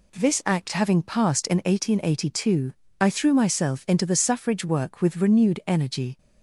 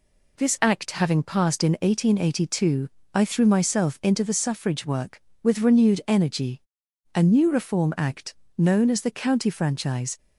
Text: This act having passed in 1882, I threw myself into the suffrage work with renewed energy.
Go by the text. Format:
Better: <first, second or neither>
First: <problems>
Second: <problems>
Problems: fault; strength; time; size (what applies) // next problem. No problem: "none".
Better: first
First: none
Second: goes on to say "A new Reform Act known as the County Franchise"; strong; from 7.1 s on; 3.0 s long